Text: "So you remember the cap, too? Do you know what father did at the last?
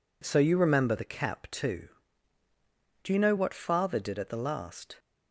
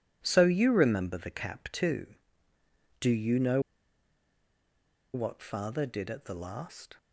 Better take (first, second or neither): first